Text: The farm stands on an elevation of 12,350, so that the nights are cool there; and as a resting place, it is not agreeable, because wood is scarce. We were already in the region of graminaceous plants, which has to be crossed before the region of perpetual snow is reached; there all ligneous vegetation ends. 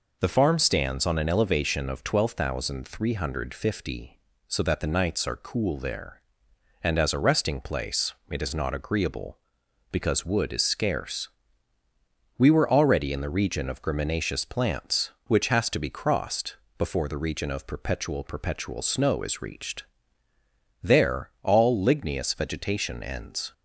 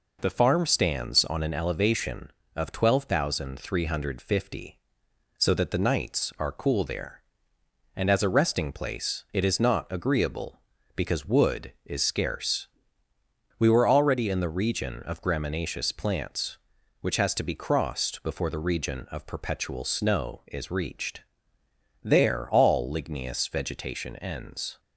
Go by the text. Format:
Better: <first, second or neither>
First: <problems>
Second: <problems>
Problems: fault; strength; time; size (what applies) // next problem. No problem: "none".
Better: second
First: pauses between "crossed" and "before"; slight; at 16.5 s; 0.24 s long // says "perpetual" twice; at 18.2 s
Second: none